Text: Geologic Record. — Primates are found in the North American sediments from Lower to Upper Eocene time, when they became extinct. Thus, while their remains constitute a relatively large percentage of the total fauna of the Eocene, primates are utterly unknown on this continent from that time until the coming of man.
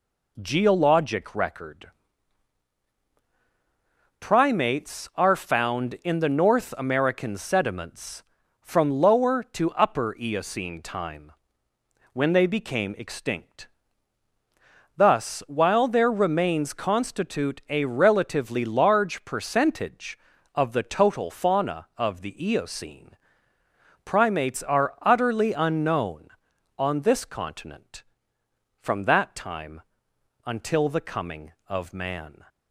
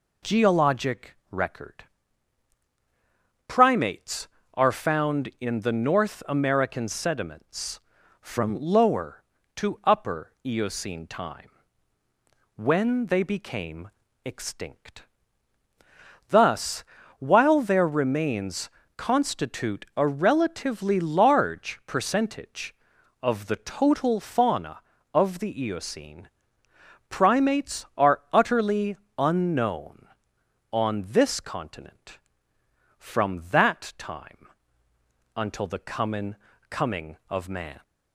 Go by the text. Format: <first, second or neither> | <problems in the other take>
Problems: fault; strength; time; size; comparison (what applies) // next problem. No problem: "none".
first | pauses between "became" and "extinct"; slight; at 13.8 s; 0.36 s long // pauses between "remains" and "constitute"; slight; at 18.6 s; 0.26 s long // pauses between "utterly" and "unknown"; slight; at 28.9 s; 0.22 s long // pauses between "time" and "until"; noticeable; at 34.4 s; 0.90 s long; noticeable in the first // says "coming" twice; at 36.7 s